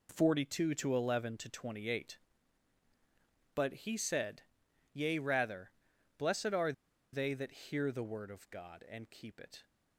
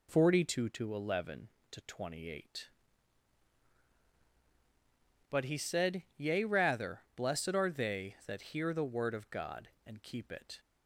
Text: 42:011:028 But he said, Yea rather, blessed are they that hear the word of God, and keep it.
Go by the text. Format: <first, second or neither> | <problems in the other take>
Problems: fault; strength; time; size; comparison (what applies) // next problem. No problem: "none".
second | pauses between "are" and "they"; at 6.7 s; 0.40 s long